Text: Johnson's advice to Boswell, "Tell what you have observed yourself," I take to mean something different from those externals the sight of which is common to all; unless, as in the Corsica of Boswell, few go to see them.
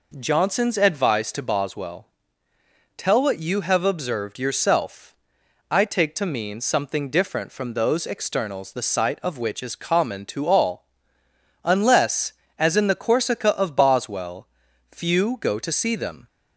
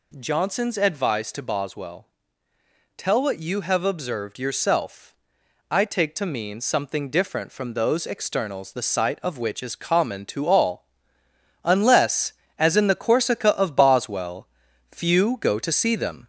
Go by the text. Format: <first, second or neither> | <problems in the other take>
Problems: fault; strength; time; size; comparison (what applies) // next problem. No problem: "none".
first | gets louder; slight; throughout; 3 dB